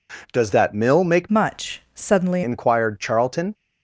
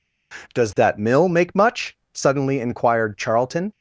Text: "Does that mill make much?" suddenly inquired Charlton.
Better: second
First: changes voice from "much" to "suddenly"; from 1.2 to 2.4 s; 1.2 s long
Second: none

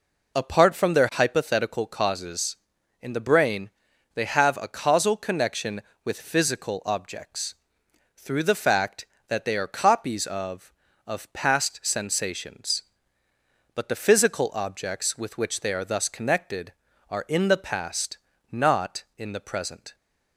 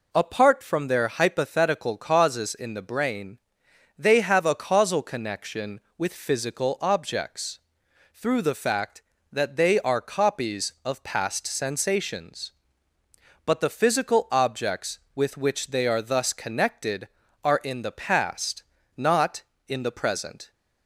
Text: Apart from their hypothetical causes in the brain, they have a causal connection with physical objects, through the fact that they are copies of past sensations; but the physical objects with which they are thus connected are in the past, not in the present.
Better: second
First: says "of" twice; at 11.0 s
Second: none

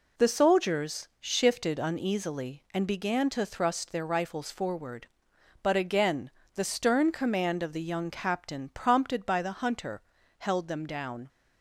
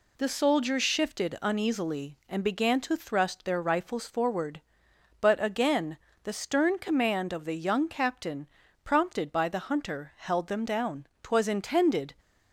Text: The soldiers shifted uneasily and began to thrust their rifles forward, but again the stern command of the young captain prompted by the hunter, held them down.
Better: first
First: pauses between "again" and "the"; slight; at 6.2 s; 0.24 s long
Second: pauses between "again" and "the"; slight; at 5.9 s; 0.26 s long // pauses between "captain" and "prompted"; at 8.4 s; 0.38 s long // goes on to say "Twas intended"; noticeable; from 11.2 s on; 0.92 s long

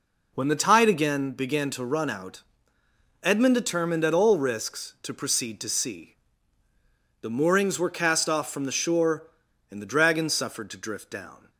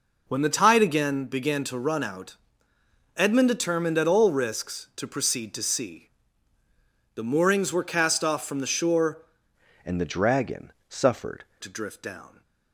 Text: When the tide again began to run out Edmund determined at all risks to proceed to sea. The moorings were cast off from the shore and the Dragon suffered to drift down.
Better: first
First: pauses between "out" and "Edmund"; noticeable; at 2.4 s; 0.80 s long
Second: pauses between "out" and "Edmund"; noticeable; at 2.3 s; 0.80 s long // changes voice from "and" to "suffered"; from 9.8 to 11.4 s; 1.6 s long // pauses between "Dragon" and "suffered"; slight; at 10.7 s; 0.18 s long

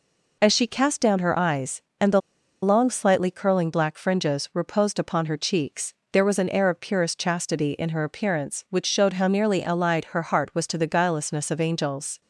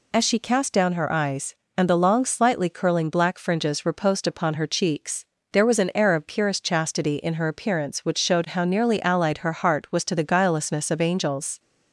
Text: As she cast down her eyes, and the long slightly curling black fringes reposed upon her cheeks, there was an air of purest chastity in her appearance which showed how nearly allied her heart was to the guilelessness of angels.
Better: second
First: pauses between "the" and "long"; at 2.2 s; 0.42 s long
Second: none

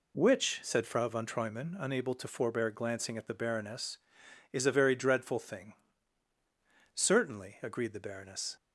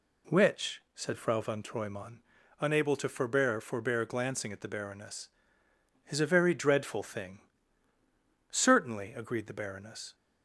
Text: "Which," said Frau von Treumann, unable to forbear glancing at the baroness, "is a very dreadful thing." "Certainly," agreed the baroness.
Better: first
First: none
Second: says "forbear" twice; at 3.6 s

